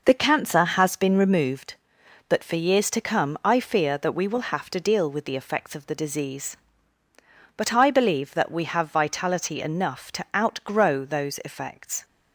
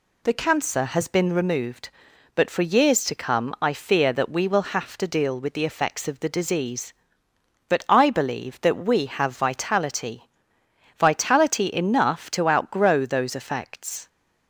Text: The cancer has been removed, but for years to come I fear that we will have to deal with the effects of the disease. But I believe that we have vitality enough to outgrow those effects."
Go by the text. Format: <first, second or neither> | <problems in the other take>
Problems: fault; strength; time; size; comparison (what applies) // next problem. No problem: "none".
first | says "vitality" twice; at 10.9 s